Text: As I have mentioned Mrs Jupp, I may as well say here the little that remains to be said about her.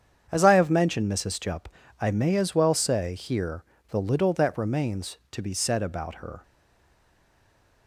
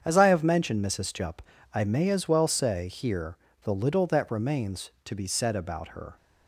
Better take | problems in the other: second | starts louder than the rest; strong; until 1.3 s; 8 dB; strong in the second // pauses between "here" and "the"; slight; at 3.6 s; 0.24 s long; slight in the second // stays silent after the last word; noticeable; from 6.4 s on; 1.4 s long

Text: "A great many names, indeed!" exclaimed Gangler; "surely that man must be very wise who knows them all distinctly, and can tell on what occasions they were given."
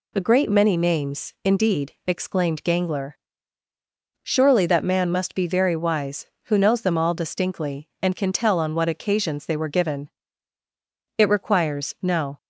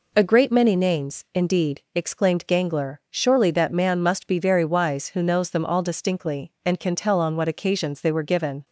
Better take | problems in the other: second | goes on to say "It requires no"; noticeable; from 11.1 s on; 1.2 s long

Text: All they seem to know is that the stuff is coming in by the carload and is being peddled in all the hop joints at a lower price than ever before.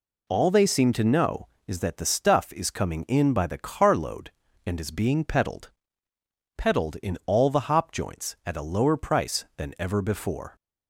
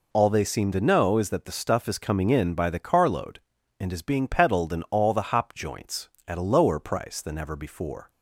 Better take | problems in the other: second | says "peddled" twice; at 6.5 s

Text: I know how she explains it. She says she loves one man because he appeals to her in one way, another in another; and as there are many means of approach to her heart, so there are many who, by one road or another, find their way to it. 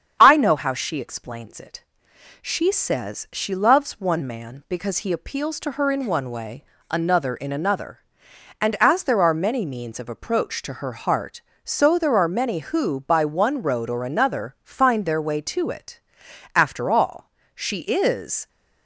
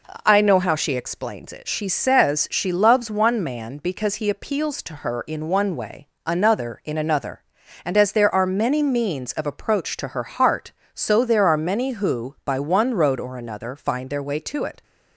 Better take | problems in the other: second | starts louder than the rest; strong; until 1.2 s; 8 dB // goes on to say "After all she is"; strong; from 16.5 s on; 1.9 s long

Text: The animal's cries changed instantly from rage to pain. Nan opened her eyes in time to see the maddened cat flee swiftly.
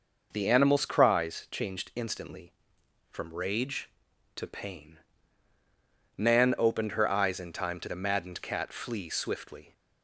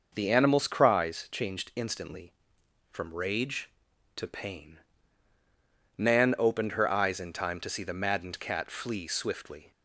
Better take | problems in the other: second | skips "see"; at 7.8 s

